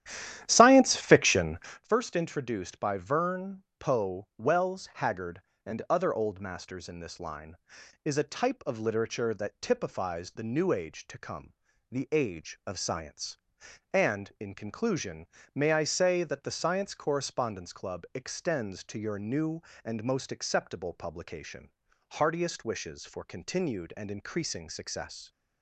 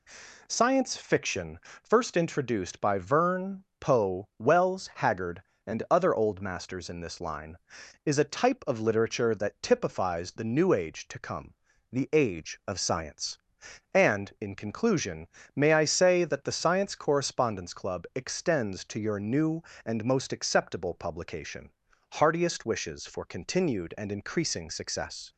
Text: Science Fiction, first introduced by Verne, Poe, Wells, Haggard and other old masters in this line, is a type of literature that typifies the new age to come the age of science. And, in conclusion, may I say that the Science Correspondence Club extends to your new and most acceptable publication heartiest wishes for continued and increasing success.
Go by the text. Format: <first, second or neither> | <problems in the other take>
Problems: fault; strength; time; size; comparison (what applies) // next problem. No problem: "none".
second | starts louder than the rest; strong; until 1.8 s; 11.5 dB // pauses between "come" and "the"; slight; at 11.5 s; 0.36 s long; slight in the second // pauses between "publication" and "heartiest"; at 21.7 s; 0.40 s long; also in the second